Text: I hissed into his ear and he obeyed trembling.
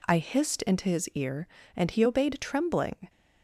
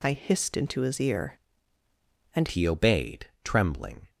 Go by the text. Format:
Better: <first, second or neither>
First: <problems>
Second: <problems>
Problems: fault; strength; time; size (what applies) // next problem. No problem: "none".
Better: first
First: none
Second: changes voice at "he"; from 2.4 s on; 1.6 s long